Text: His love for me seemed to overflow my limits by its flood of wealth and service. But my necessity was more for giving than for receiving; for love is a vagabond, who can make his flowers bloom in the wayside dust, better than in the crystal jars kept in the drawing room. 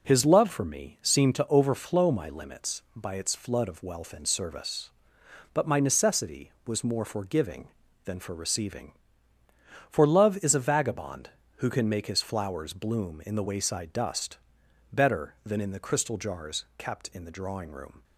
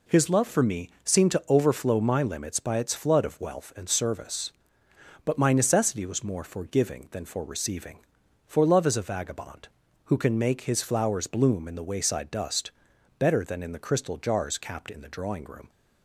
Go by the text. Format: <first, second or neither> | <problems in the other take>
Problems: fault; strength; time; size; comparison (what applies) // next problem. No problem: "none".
first | says "capped" for "kept"; at 14.5 s